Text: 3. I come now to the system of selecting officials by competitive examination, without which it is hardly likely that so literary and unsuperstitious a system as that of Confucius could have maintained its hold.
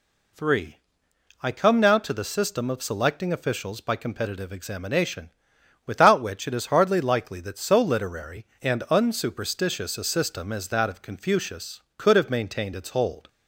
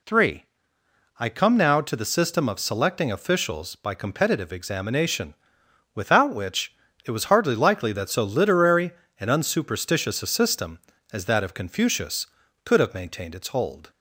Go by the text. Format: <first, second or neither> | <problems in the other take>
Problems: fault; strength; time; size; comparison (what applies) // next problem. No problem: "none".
first | pauses between "which" and "it"; slight; at 6.7 s; 0.30 s long // says "was" for "is"; at 7.1 s